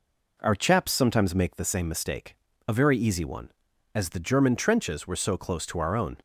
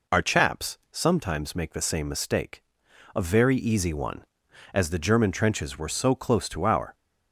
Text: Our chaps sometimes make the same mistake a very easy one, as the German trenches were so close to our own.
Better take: first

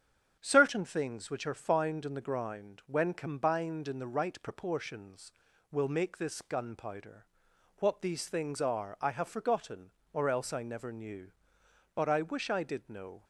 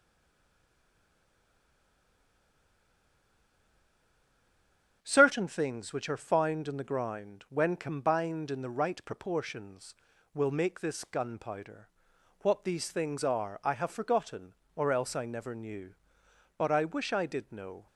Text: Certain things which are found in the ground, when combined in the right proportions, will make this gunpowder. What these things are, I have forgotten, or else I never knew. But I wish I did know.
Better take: first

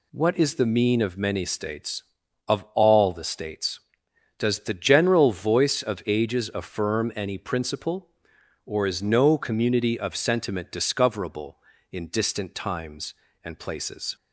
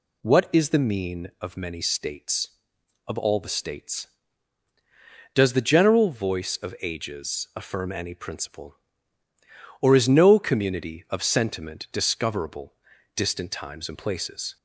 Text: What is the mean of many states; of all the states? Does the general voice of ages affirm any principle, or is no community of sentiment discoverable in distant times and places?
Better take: first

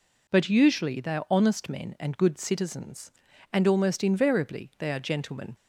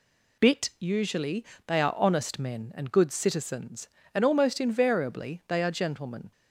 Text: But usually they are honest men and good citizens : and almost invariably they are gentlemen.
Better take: first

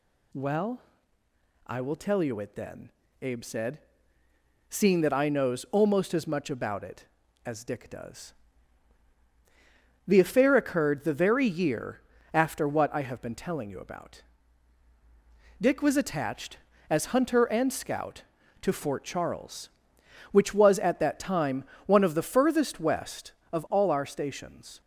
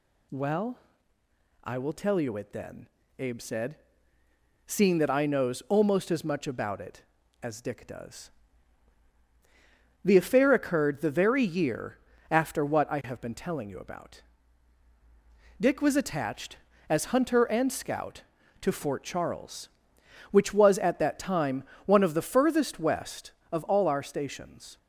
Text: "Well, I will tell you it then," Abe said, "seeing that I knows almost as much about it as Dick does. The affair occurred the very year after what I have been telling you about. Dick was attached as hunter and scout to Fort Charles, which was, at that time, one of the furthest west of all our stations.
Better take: neither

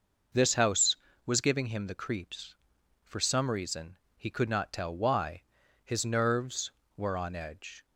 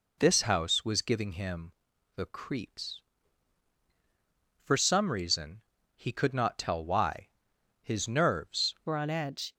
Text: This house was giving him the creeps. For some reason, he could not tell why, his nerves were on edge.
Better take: first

